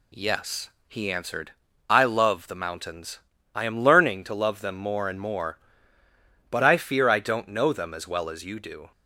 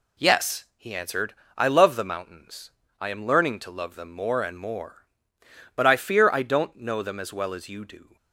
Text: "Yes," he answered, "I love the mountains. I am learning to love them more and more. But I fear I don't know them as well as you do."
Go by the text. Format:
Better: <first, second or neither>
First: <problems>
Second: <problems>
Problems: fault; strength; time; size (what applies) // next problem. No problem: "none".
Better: neither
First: none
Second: none